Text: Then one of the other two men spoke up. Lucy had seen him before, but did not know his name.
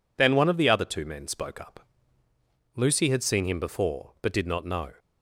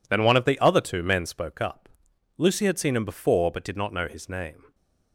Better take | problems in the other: second | stops before "his name"; at 4.9 s

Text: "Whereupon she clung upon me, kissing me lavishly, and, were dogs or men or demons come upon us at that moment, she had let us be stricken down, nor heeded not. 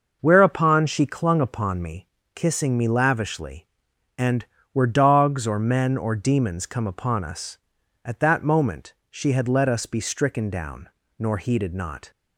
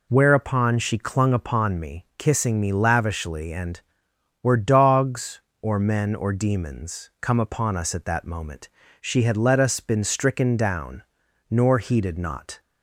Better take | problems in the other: first | says "been" for "be"; at 9.7 s

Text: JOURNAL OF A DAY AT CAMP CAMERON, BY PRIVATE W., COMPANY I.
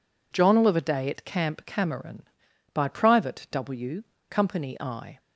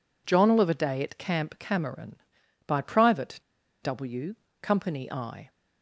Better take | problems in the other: first | pauses between "PRIVATE" and "W"; at 3.4 s; 0.42 s long

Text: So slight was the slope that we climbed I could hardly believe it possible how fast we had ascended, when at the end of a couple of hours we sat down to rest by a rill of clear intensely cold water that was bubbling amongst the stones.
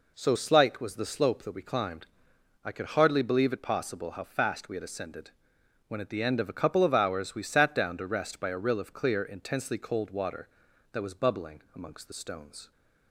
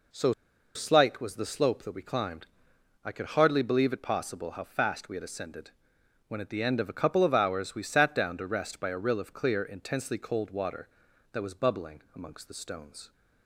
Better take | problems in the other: first | pauses between "So" and "slight"; at 0.3 s; 0.42 s long // pauses between "climbed" and "I"; noticeable; at 2.4 s; 0.60 s long; noticeable in the first

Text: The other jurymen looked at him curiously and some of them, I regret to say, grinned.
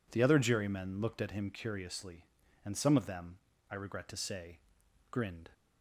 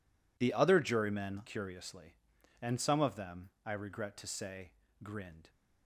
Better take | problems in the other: first | skips "looked at him"; at 1.4 s

